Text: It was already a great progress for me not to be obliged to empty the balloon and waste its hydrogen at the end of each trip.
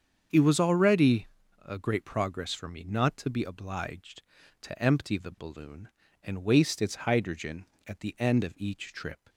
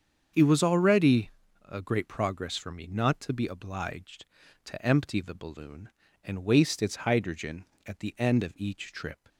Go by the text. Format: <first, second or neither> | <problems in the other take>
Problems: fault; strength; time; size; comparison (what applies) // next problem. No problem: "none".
neither | starts louder than the rest; strong; the same in both // pauses between "already" and "a"; the same in both